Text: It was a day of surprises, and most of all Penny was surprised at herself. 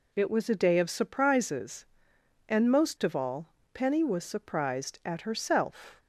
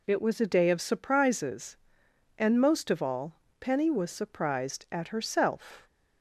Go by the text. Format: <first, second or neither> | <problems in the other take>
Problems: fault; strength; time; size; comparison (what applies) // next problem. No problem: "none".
neither | pauses between "all" and "Penny"; slight; the same in both